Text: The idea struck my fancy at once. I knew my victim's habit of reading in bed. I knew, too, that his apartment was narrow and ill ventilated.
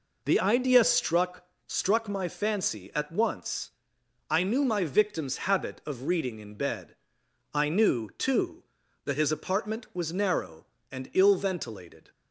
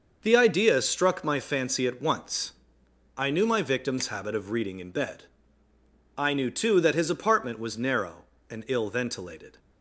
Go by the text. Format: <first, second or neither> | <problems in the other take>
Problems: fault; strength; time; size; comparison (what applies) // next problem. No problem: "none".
second | says "struck" twice; at 1.6 s